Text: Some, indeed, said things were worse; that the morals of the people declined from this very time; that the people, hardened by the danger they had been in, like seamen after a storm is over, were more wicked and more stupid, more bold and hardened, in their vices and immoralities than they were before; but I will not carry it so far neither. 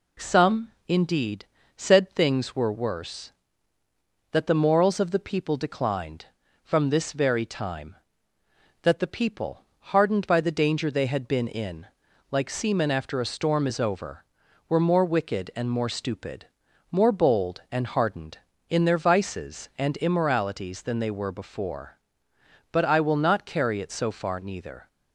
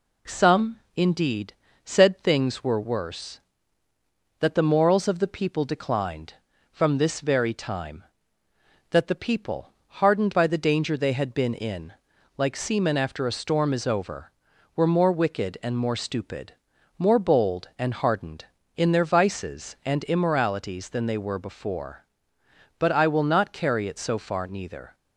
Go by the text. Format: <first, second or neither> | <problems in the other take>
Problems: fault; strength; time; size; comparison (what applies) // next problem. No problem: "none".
neither | none